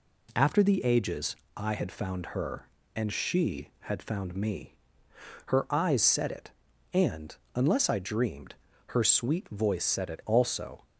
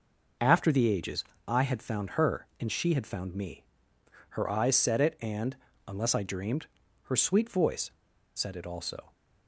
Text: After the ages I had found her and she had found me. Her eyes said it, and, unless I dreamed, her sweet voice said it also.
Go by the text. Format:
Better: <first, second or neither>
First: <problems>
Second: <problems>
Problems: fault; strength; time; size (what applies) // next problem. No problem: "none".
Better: first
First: pauses between "ages" and "I"; slight; at 1.3 s; 0.21 s long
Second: pauses between "ages" and "I"; slight; at 1.2 s; 0.24 s long // pauses between "voice" and "said"; at 7.8 s; 0.44 s long